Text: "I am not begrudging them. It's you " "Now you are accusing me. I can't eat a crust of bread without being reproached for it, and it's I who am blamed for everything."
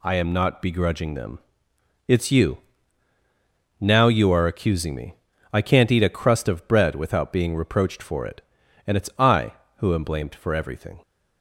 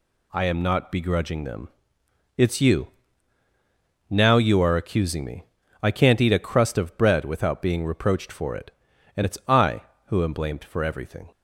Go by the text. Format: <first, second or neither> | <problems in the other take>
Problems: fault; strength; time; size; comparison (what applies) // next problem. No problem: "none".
neither | none